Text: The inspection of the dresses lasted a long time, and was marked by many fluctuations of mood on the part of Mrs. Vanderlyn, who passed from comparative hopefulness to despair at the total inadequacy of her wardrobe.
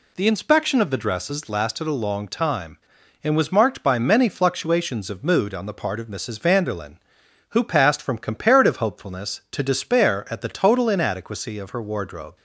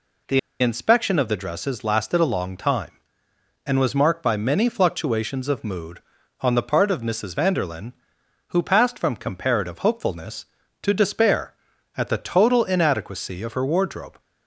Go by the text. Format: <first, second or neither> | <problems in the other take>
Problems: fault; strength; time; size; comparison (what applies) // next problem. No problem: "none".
first | pauses between "The" and "inspection"; slight; at 0.3 s; 0.22 s long